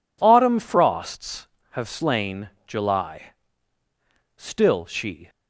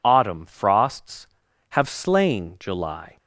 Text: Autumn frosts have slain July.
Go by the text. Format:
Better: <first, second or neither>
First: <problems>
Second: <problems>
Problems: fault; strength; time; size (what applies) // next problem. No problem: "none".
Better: second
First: pauses between "slain" and "July"; slight; at 2.4 s; 0.18 s long // goes on to say "Still she"; noticeable; from 4.3 s on; 0.94 s long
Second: none